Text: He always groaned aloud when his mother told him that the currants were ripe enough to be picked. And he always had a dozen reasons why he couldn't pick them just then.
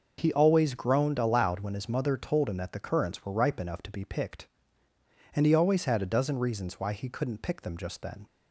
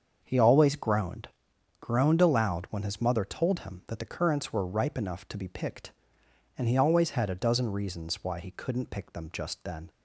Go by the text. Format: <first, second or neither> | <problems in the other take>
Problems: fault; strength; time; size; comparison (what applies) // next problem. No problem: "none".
first | starts louder than the rest; until 1.2 s; 7 dB // says "groaned" twice; at 1.7 s